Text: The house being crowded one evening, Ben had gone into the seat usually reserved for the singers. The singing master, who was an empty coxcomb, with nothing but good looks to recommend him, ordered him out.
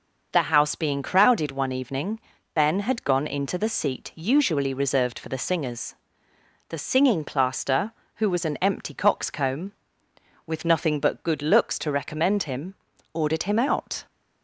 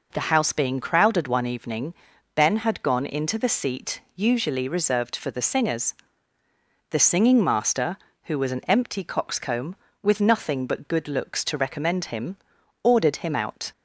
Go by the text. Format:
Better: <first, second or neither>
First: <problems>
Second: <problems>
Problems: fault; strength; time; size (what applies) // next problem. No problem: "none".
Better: second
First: says "plaster" for "master"; at 7.2 s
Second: none